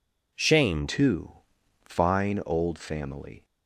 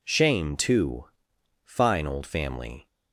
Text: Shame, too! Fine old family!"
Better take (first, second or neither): second